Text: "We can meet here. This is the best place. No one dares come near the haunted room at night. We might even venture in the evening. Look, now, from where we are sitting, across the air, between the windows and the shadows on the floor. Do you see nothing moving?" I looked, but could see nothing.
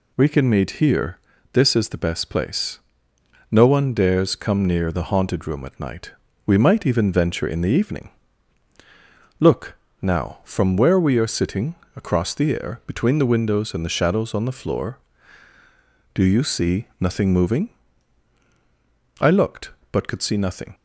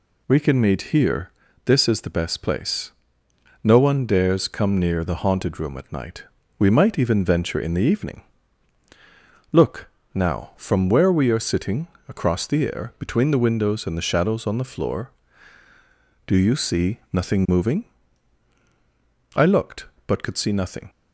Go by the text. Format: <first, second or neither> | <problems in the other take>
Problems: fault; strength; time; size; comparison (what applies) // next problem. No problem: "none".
neither | none